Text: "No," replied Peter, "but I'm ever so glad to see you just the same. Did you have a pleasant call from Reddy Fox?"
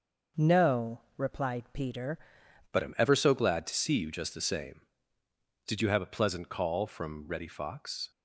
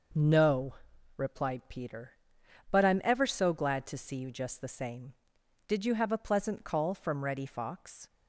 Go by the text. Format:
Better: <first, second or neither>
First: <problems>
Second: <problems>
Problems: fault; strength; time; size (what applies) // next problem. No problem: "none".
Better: second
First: changes voice at "but"; from 2.7 s on; 5.4 s long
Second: none